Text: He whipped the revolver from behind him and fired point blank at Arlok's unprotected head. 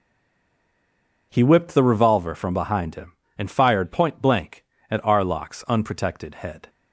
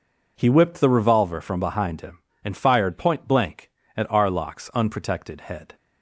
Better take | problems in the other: second | stays silent before the first word; noticeable; until 1.3 s; 1.3 s long

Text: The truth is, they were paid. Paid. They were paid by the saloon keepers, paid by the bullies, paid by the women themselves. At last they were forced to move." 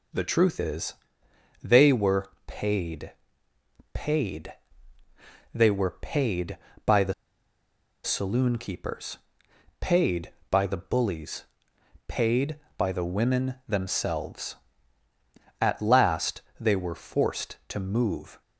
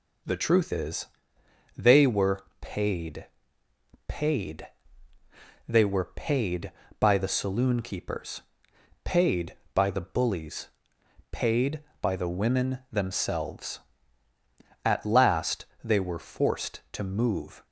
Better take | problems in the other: second | pauses between "were" and "paid"; slight; at 2.2 s; 0.18 s long; slight in the second // pauses between "the" and "saloon"; noticeable; at 7.1 s; 0.91 s long // pauses between "last" and "they"; slight; at 16.4 s; 0.18 s long; slight in the second

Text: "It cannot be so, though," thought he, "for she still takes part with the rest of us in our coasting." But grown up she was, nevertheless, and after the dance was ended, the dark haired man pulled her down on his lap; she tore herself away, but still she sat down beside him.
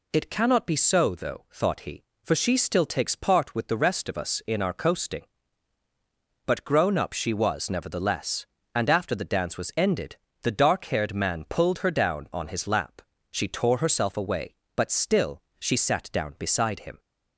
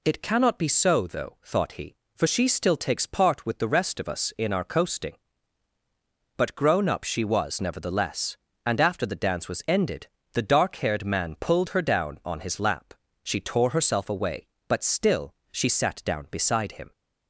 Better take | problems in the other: neither | pauses between "still" and "she"; slight; the same in both

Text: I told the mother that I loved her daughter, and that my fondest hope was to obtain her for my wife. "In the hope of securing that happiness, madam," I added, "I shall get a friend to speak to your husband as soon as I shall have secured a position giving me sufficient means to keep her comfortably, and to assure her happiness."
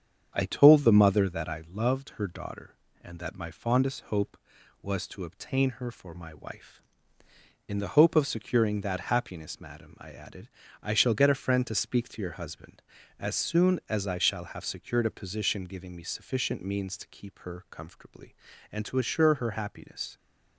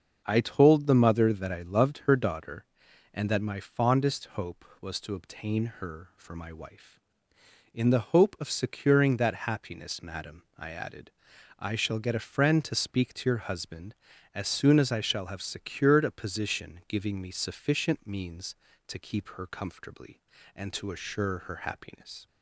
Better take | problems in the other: neither | starts louder than the rest; the same in both

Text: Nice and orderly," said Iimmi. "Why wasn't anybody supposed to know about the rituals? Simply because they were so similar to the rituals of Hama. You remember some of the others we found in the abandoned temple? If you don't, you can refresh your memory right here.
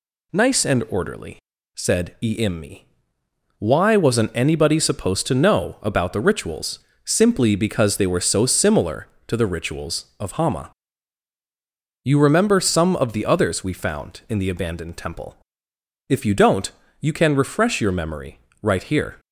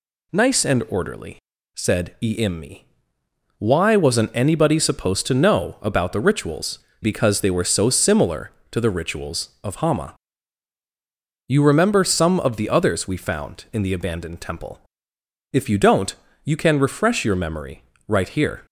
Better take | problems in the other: first | skips "Simply"; at 6.8 s // pauses between "memory" and "right"; slight; at 17.8 s; 0.26 s long; slight in the first

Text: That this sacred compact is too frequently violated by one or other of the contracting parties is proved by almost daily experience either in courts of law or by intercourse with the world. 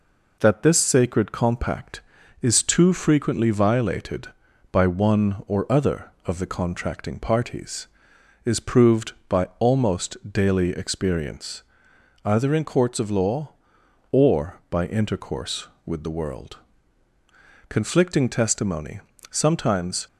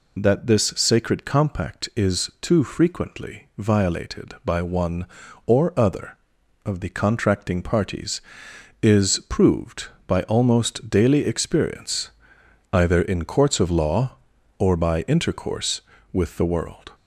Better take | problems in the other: second | pauses between "experience" and "either"; noticeable; at 11.6 s; 0.62 s long; noticeable in the second // goes on to say "Conflicting testimony sometimes"; strong; from 17.6 s on; 2.3 s long

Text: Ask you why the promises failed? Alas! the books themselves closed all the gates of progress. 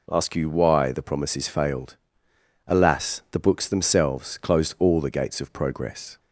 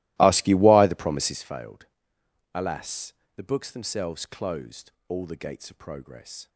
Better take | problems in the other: first | starts louder than the rest; strong; until 1.4 s; 18.5 dB // pauses between "closed" and "all"; slight; at 4.9 s; 0.16 s long

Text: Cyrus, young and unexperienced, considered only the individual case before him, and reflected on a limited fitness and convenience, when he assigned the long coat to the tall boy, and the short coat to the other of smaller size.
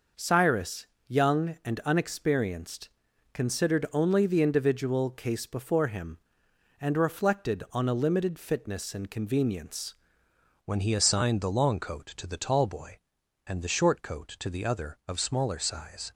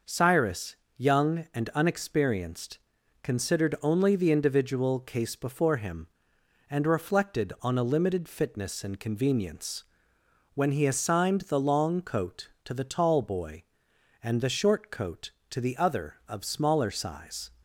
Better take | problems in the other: second | changes voice at "when"; from 10.6 s on; 5.5 s long

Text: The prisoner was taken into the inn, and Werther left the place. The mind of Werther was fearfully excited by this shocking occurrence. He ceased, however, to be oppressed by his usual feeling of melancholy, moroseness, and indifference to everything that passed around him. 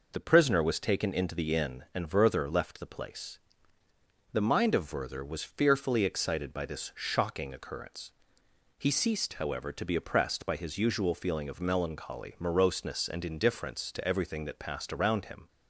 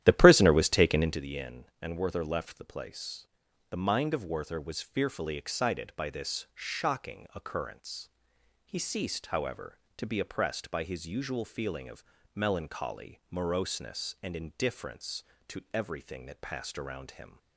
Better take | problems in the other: first | starts louder than the rest; strong; until 1.3 s; 12 dB // pauses between "of" and "melancholy"; slight; at 12.0 s; 0.30 s long

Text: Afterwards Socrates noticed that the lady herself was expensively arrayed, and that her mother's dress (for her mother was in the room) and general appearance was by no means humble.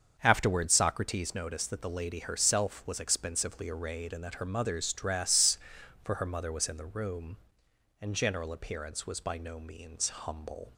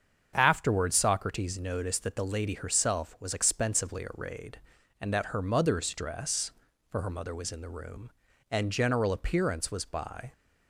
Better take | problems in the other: first | starts louder than the rest; strong; until 1.3 s; 7 dB; also in the first // stops before "no means humble"; at 10.3 s

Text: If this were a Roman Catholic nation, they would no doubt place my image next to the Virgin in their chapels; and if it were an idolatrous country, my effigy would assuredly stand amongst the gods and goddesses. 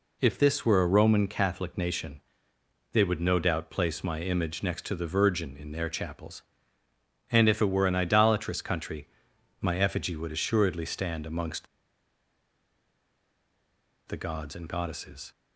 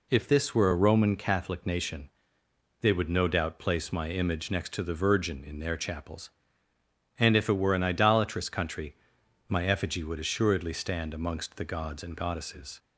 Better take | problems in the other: second | pauses between "amongst" and "the"; strong; at 11.6 s; 2.4 s long

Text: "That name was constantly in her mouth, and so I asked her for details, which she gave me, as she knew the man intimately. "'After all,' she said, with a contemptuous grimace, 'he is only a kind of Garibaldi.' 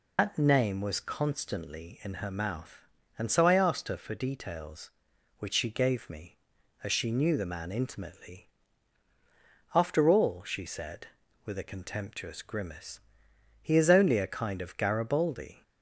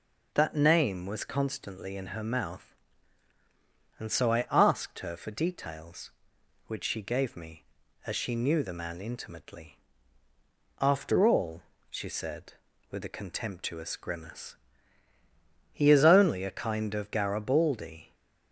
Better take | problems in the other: second | loses the start of "That"; at 0.1 s; 105 ms

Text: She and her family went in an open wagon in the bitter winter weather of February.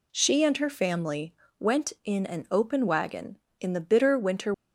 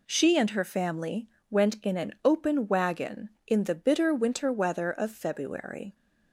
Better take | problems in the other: second | pauses between "family" and "went"; slight; at 1.3 s; 0.24 s long; slight in the second // stops before "weather of February"; at 4.5 s

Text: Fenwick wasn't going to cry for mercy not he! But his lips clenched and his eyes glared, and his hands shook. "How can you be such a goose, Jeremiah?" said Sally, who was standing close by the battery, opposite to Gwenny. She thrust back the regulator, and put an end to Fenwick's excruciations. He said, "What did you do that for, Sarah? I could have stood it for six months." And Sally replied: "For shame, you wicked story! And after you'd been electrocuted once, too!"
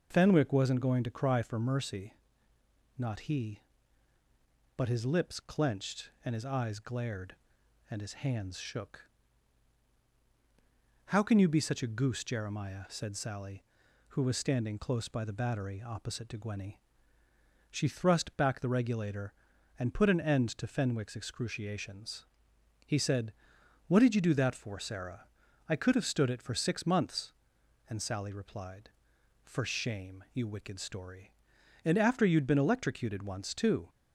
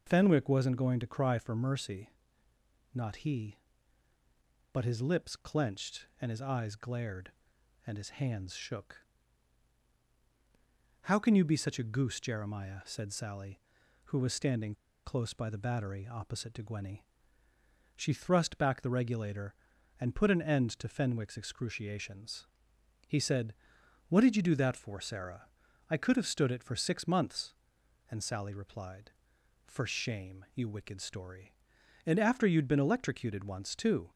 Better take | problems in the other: first | pauses between "mercy" and "not"; noticeable; at 2.1 s; 0.82 s long; noticeable in the first // pauses between "standing" and "close"; slight; at 14.7 s; 0.31 s long

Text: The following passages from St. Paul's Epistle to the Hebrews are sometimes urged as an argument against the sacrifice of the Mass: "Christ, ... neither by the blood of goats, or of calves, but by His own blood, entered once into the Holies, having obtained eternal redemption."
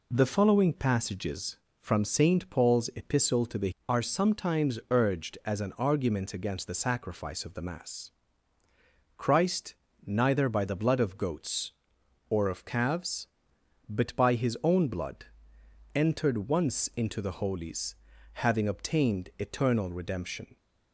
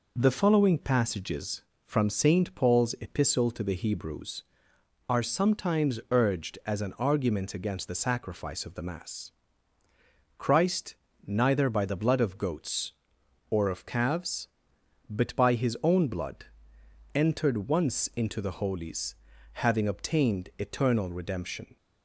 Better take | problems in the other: second | skips "Hebrews"; at 3.7 s

